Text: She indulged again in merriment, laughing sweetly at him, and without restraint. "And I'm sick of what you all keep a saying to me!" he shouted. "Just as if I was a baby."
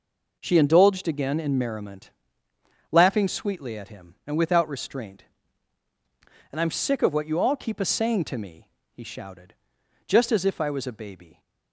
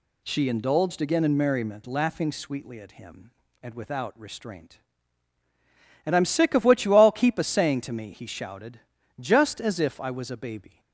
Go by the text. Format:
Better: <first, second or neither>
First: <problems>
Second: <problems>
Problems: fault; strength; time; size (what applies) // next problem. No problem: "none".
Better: neither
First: none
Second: none